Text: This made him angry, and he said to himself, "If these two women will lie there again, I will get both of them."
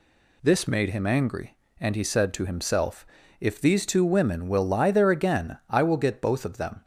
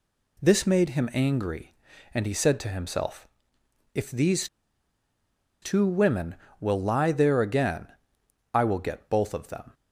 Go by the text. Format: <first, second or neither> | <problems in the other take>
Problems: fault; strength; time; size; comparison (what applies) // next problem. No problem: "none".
first | pauses between "these" and "two"; at 4.4 s; 1.1 s long